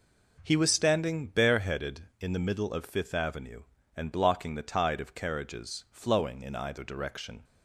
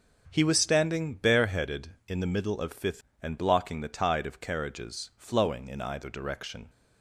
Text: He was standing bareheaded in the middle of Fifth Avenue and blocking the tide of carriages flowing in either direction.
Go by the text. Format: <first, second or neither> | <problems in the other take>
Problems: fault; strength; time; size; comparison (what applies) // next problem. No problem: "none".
first | starts louder than the rest; until 1.3 s; 6.5 dB // skips "Avenue"; at 3.1 s